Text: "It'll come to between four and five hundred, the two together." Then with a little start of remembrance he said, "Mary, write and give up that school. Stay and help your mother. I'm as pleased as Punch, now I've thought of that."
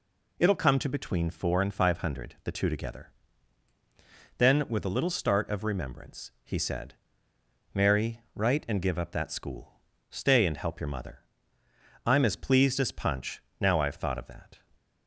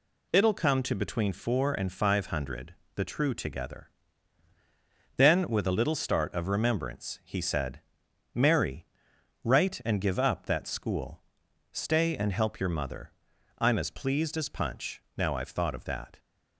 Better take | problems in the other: first | says "true" for "two"; at 3.0 s

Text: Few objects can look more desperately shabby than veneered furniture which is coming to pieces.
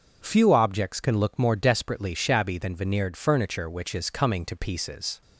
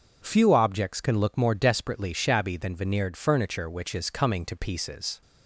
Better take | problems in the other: neither | none

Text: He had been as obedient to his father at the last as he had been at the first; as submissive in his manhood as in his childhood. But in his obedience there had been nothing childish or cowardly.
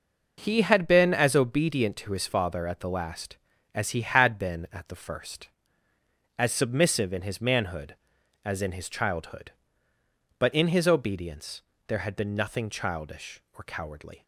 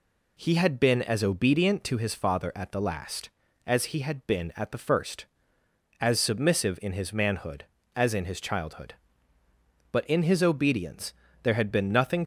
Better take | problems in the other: first | pauses between "obedience" and "there"; slight; at 11.1 s; 0.30 s long; slight in the first // stops before "childish or cowardly"; at 12.2 s

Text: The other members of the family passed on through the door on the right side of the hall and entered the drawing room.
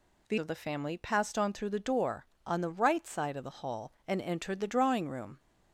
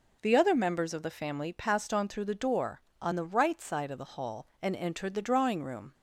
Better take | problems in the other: second | skips "other members"; at 0.3 s

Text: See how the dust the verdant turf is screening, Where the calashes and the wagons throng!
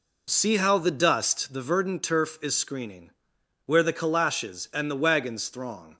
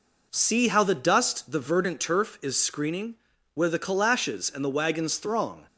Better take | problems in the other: neither | none

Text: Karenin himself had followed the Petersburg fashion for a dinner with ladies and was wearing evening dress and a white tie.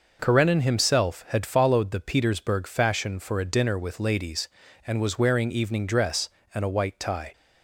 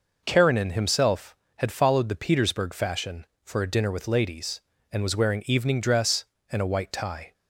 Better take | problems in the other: neither | none

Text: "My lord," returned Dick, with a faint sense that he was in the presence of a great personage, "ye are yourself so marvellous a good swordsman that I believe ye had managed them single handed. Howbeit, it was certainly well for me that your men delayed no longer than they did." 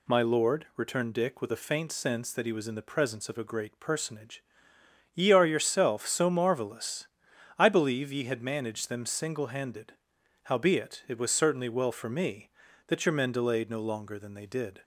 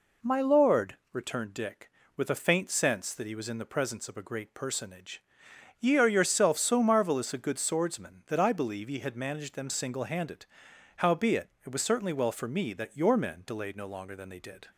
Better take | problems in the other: second | skips "a good swordsman that"; at 7.3 s

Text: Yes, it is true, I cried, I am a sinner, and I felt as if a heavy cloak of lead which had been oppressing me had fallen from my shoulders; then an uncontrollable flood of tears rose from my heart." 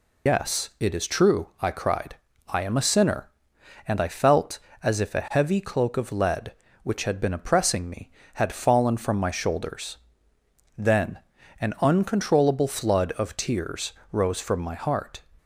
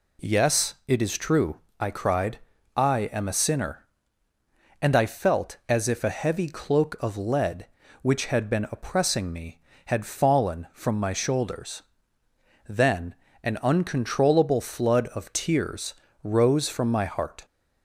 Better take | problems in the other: second | loses the start of "Yes"; at 0.2 s; 105 ms // pauses between "then" and "an"; at 11.1 s; 0.40 s long; slight in the second // pauses between "tears" and "rose"; slight; at 13.9 s; 0.22 s long; slight in the second

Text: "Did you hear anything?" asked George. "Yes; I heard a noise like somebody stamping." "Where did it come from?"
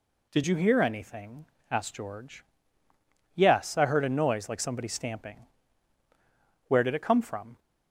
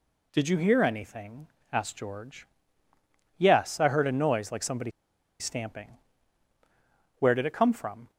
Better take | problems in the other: first | pauses between "somebody" and "stamping"; noticeable; at 4.9 s; 0.48 s long

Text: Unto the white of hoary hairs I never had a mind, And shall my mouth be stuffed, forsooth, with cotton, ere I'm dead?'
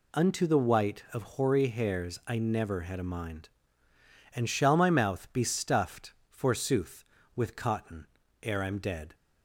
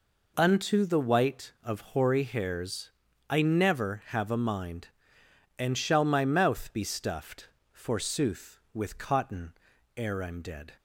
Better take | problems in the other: first | pauses between "hairs" and "I"; at 2.8 s; 0.40 s long // says "have" for "had"; at 4.0 s

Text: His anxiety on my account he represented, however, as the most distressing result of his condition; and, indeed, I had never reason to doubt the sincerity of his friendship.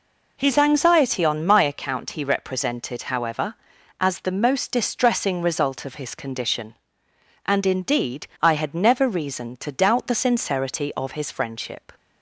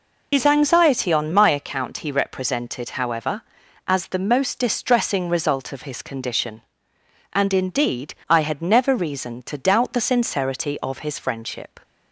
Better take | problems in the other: first | loses the start of "His"; at 0.3 s; 75 ms

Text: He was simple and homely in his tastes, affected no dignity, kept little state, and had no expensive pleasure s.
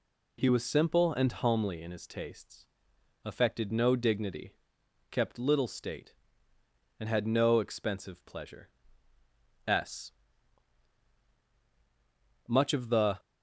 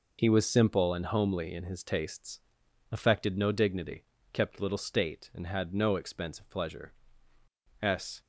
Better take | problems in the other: second | pauses between "pleasure" and "s"; noticeable; at 8.6 s; 0.98 s long; noticeable in the second // goes on to say "Much of the"; noticeable; from 12.4 s on; 0.72 s long

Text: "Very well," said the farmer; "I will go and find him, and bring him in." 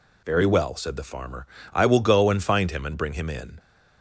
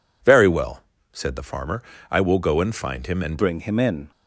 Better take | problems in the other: first | changes voice at "bring"; from 3.3 s on; 0.8 s long

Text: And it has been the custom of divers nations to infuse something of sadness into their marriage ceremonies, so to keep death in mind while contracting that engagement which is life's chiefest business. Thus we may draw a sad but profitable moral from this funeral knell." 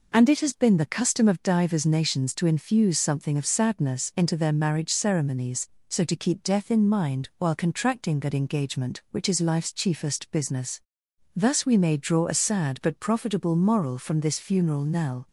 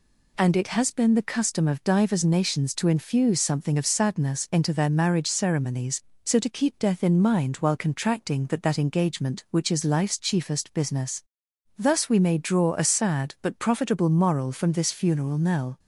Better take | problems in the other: first | says "that" twice; at 8.6 s

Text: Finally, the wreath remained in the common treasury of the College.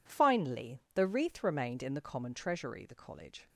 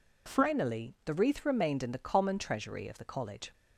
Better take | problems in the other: second | skips "of"; at 2.8 s

